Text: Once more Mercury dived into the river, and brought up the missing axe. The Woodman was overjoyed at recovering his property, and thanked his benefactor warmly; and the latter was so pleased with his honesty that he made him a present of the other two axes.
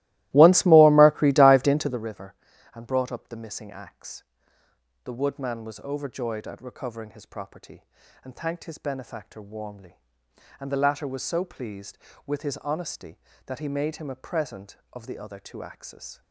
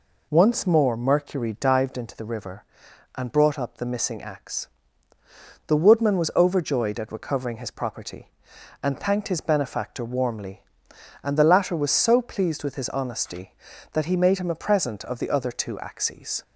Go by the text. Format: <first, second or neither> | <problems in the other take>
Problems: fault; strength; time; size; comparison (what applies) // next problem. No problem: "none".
second | starts louder than the rest; strong; until 2.1 s; 17.5 dB